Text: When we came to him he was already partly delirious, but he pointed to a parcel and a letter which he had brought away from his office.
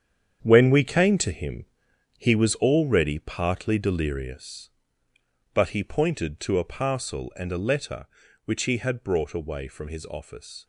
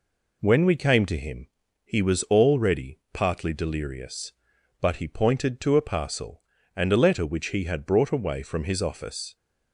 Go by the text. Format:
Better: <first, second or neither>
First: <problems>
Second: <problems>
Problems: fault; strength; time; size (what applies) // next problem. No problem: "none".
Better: second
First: gets quieter; strong; throughout; 10 dB // pauses between "him" and "he"; noticeable; at 1.6 s; 0.52 s long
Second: pauses between "him" and "he"; slight; at 1.4 s; 0.36 s long